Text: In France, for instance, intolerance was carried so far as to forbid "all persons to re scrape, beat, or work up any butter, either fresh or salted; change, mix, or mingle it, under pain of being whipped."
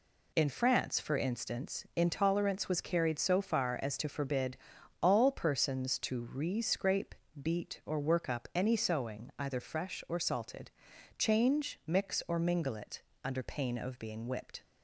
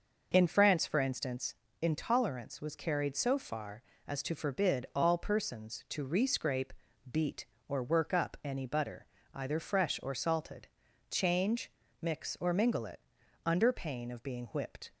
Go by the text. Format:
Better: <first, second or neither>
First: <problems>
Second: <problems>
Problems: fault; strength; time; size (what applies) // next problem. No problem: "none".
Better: second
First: pauses between "forbid" and "all"; noticeable; at 4.5 s; 0.46 s long // says "sewing" for "butter"; at 8.7 s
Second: none